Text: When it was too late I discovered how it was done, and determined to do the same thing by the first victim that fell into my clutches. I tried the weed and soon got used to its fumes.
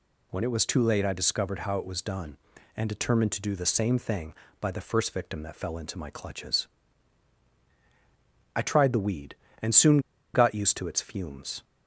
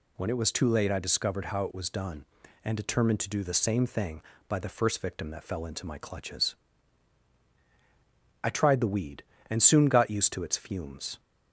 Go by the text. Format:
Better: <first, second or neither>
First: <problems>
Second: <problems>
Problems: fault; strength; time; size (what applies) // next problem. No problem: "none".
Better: second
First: pauses between "soon" and "got"; slight; at 9.9 s; 0.34 s long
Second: none